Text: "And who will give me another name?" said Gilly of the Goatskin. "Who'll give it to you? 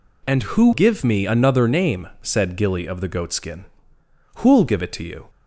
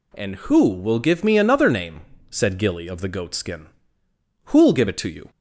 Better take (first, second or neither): second